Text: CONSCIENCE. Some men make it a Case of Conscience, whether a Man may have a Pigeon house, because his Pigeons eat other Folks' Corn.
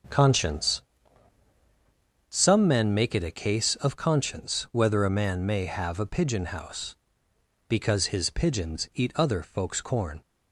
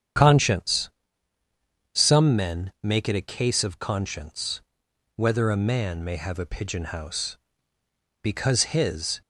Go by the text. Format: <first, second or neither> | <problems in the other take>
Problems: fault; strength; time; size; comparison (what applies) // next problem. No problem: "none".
first | starts louder than the rest; strong; until 2.2 s; 8.5 dB; also in the first // stops before "Pigeons eat other Folks Corn"; at 9.2 s